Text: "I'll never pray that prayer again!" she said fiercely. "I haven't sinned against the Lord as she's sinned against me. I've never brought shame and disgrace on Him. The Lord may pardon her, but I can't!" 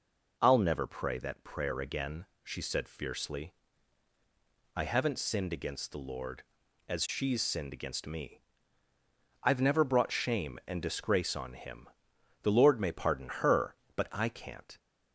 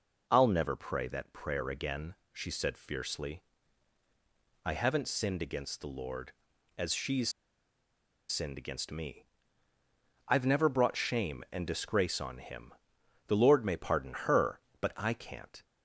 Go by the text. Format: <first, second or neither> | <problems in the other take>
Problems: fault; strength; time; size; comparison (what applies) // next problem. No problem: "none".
first | pauses between "she's" and "sinned"; at 7.2 s; 1.0 s long